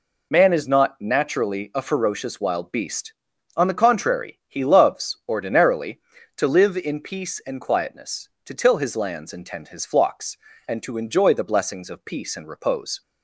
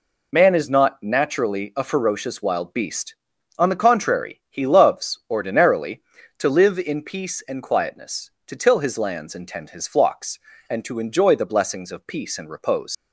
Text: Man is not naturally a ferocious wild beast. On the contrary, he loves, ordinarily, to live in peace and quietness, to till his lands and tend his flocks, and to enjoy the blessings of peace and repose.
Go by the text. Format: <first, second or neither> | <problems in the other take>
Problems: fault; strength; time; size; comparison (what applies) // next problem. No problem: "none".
first | leaves "repose" unfinished; at 12.9 s; 80 ms